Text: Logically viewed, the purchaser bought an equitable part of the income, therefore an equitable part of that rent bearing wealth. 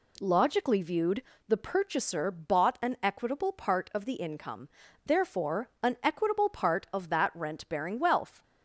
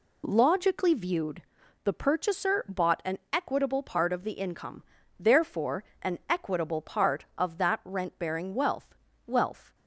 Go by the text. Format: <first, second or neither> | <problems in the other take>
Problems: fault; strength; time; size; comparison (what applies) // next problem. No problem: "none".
first | pauses between "therefore" and "an"; slight; at 5.8 s; 0.18 s long // says "wealth" twice; at 9.2 s